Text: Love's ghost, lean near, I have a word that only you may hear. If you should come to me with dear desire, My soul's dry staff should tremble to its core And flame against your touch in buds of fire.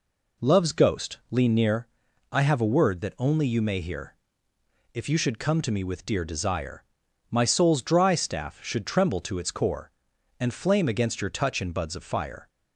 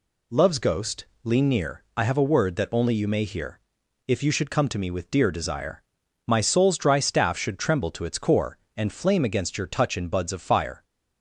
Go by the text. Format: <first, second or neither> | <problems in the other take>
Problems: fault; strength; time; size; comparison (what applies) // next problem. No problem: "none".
neither | none